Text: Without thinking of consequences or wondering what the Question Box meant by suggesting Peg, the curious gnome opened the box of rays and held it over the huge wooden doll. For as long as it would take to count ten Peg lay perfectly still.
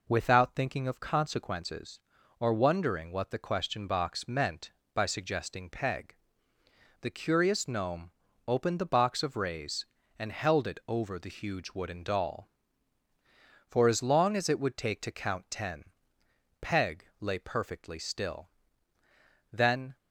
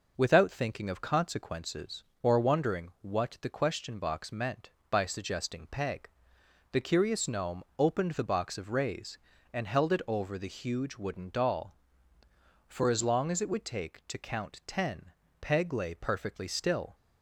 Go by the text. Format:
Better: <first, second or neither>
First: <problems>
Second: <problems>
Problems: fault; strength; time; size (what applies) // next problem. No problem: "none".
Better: second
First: pauses between "gnome" and "opened"; slight; at 8.1 s; 0.36 s long // pauses between "ten" and "Peg"; noticeable; at 15.8 s; 0.78 s long // pauses between "Peg" and "lay"; slight; at 17.0 s; 0.16 s long // goes on to say "Then"; slight; from 19.5 s on; 0.46 s long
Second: pauses between "ten" and "Peg"; slight; at 15.1 s; 0.30 s long